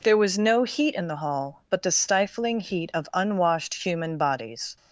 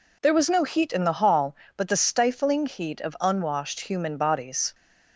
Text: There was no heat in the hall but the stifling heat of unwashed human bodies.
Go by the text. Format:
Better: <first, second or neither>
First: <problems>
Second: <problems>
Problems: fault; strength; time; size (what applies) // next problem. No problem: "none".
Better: neither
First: none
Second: none